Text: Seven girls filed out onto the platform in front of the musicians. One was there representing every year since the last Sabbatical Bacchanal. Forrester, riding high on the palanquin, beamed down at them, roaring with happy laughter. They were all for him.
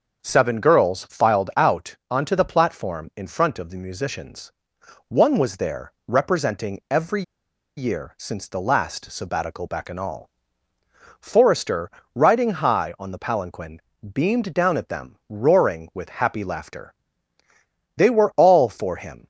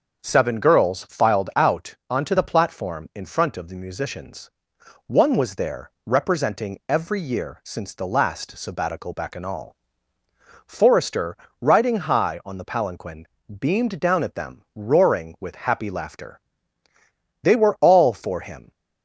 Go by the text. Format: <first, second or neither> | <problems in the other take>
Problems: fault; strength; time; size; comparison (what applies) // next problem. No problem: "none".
second | pauses between "every" and "year"; noticeable; at 7.2 s; 0.55 s long